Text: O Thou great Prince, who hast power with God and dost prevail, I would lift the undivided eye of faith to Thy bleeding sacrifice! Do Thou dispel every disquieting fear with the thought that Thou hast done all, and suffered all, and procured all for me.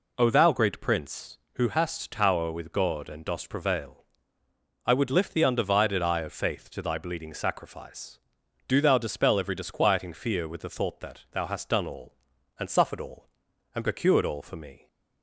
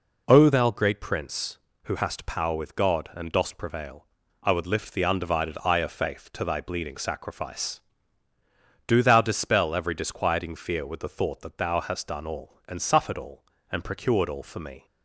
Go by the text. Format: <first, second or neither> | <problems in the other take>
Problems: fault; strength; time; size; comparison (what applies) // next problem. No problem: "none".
second | says "tower" for "power"; at 2.0 s